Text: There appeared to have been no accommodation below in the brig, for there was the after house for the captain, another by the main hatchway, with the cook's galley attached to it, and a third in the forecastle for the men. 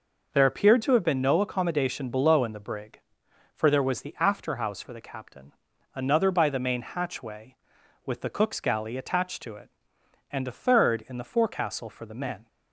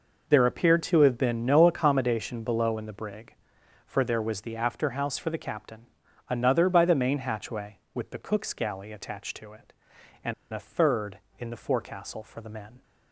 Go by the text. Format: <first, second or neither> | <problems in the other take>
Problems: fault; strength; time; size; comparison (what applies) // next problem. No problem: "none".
first | pauses between "and" and "a"; slight; at 10.3 s; 0.18 s long